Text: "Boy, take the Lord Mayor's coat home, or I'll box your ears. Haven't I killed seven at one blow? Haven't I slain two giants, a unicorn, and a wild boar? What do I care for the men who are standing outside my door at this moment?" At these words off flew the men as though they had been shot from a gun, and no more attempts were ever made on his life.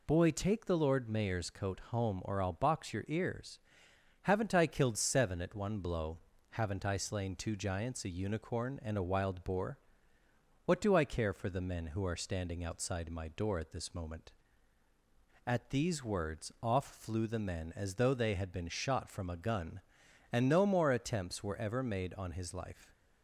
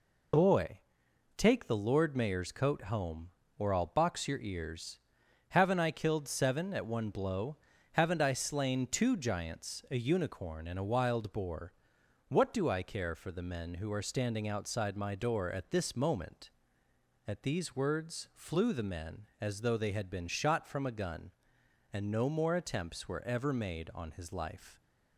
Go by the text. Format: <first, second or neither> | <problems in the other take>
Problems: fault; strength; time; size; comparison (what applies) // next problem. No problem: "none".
first | skips "off"; at 18.2 s